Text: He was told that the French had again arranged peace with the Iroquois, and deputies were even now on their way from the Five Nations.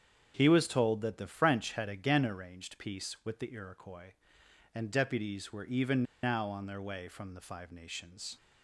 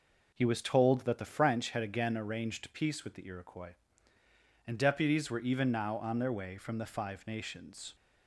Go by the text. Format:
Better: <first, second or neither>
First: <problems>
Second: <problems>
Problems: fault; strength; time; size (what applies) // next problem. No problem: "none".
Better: second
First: starts louder than the rest; strong; until 1.3 s; 7.5 dB // pauses between "even" and "now"; slight; at 6.0 s; 0.19 s long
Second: none